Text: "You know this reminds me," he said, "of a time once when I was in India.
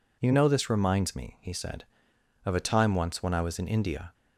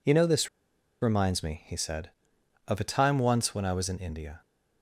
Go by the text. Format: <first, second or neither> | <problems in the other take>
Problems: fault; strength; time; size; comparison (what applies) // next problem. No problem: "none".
first | pauses between "this" and "reminds"; noticeable; at 0.4 s; 0.53 s long